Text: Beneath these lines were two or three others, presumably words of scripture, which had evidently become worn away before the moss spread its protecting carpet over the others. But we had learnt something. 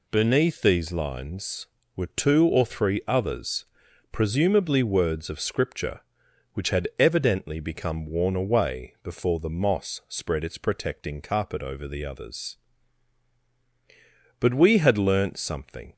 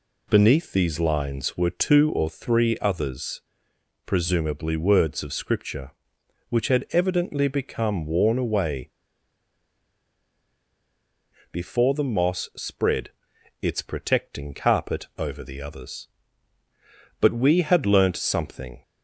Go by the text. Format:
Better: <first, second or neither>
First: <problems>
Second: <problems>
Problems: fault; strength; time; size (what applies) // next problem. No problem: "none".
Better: first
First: none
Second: pauses between "away" and "before"; strong; at 8.9 s; 2.6 s long // pauses between "spread" and "its"; noticeable; at 13.0 s; 0.50 s long